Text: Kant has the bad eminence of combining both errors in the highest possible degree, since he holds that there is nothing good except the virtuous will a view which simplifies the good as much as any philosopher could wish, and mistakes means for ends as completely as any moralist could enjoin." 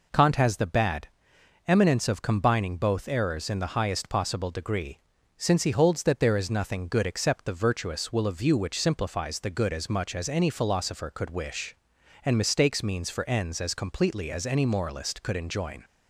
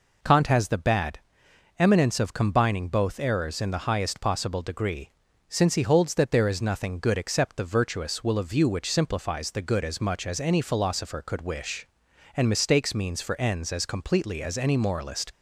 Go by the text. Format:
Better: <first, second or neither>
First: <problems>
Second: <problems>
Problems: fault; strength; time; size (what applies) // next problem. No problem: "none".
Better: first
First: pauses between "bad" and "eminence"; noticeable; at 1.0 s; 0.60 s long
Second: pauses between "bad" and "eminence"; noticeable; at 1.1 s; 0.60 s long // stops before "could enjoin"; at 15.3 s